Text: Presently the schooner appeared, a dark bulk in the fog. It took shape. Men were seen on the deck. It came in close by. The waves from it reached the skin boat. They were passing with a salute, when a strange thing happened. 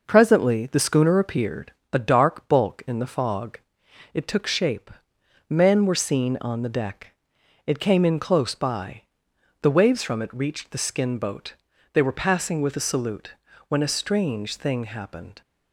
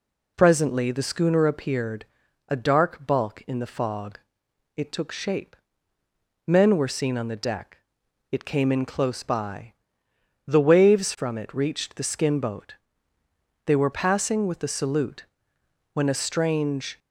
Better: first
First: none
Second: stops before "thing happened"; at 16.9 s

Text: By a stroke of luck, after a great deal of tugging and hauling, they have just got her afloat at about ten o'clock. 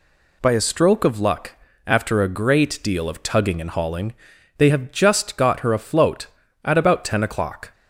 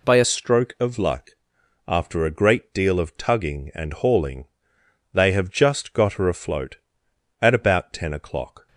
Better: first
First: none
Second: changes voice at "stroke"; from 0.2 s on; 8.4 s long

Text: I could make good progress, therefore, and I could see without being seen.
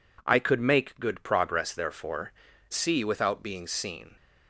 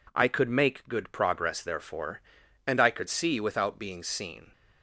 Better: second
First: skips "and I could"; at 2.5 s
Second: none

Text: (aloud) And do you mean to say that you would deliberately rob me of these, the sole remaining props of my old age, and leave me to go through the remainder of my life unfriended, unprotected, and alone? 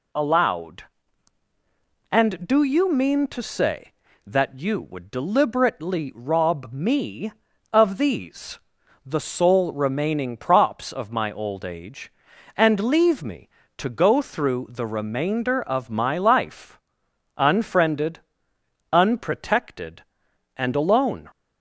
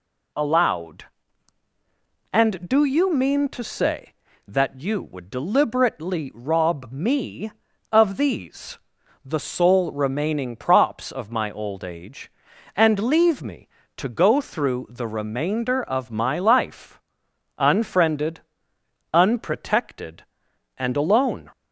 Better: neither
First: pauses between "life" and "unfriended"; noticeable; at 16.7 s; 0.62 s long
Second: pauses between "life" and "unfriended"; noticeable; at 16.9 s; 0.62 s long

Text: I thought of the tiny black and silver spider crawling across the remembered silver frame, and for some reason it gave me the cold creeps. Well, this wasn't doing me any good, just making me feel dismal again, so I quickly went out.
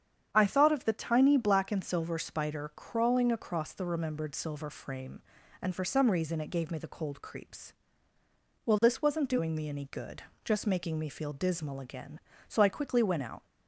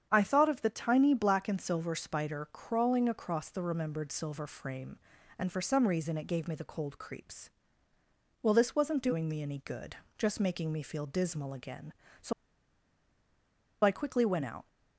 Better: first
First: starts louder than the rest; strong; until 1.3 s; 8 dB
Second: starts louder than the rest; strong; until 1.1 s; 8 dB // pauses between "so" and "I"; strong; at 12.3 s; 1.5 s long

